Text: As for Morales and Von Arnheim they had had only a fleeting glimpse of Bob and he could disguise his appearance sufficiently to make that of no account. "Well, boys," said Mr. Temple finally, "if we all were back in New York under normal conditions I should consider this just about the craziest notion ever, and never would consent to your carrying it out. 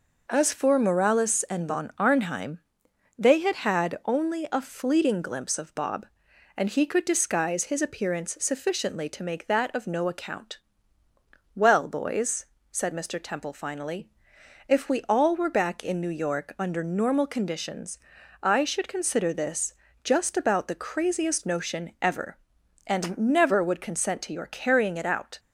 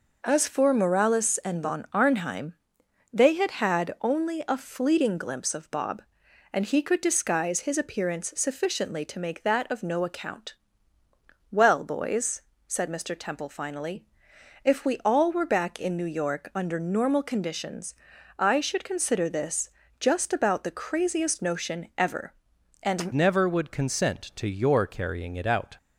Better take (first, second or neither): first